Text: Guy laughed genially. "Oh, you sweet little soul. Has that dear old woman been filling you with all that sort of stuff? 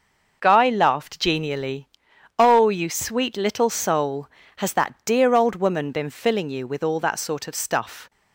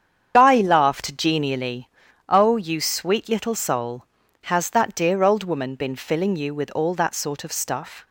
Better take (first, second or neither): first